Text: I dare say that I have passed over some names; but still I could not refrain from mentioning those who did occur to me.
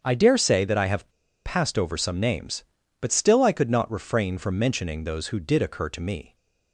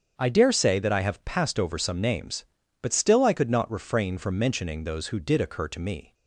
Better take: second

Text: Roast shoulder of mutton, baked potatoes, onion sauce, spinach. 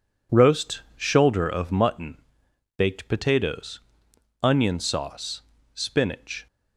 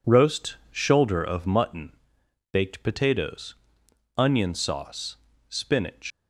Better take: first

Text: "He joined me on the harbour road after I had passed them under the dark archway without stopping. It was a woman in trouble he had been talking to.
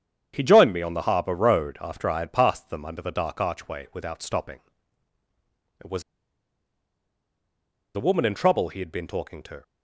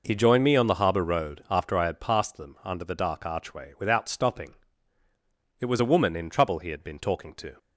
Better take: second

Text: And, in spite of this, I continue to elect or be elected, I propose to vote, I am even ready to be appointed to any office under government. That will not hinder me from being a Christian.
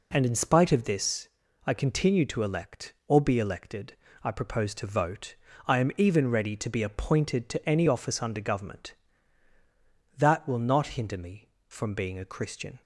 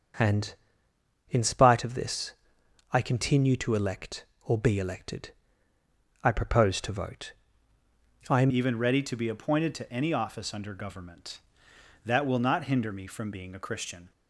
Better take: first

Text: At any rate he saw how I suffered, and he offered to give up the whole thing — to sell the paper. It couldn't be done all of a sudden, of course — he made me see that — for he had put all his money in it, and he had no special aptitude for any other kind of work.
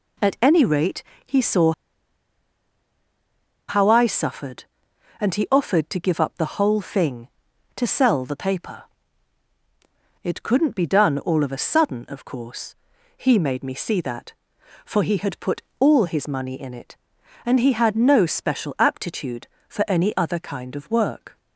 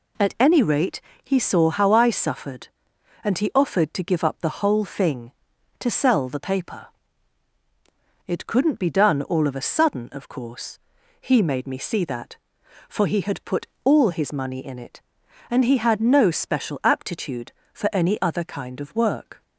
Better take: second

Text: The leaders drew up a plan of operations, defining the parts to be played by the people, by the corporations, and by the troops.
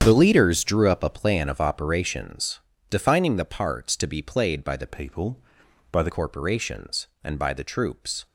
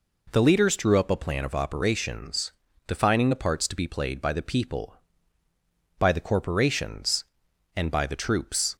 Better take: second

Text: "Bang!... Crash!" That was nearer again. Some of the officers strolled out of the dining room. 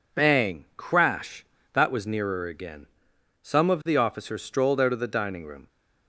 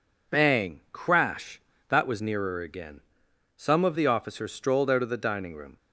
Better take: neither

